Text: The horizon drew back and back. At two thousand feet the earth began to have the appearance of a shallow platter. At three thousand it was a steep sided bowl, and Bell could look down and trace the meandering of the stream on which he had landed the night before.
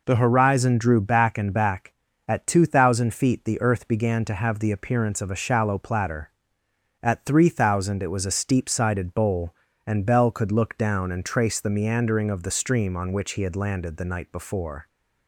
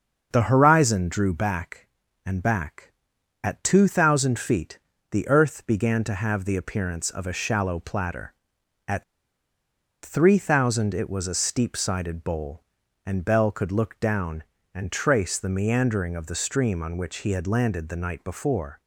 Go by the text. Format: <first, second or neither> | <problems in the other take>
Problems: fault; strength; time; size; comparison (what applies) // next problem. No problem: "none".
first | starts louder than the rest; until 1.3 s; 6.5 dB // pauses between "feet" and "the"; slight; at 4.7 s; 0.32 s long // pauses between "At" and "three"; at 9.0 s; 1.0 s long